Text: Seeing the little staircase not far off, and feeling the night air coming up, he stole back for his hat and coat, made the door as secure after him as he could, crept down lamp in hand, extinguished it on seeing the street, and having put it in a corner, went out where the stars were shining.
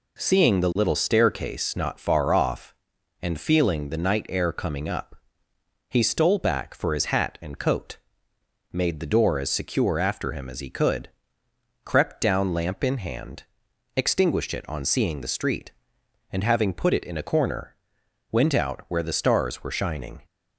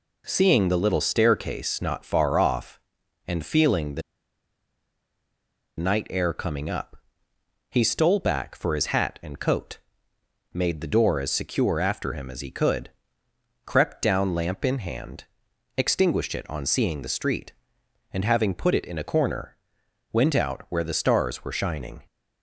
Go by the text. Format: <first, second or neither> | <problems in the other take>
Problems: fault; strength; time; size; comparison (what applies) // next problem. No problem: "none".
first | pauses between "the" and "night"; strong; at 4.0 s; 1.7 s long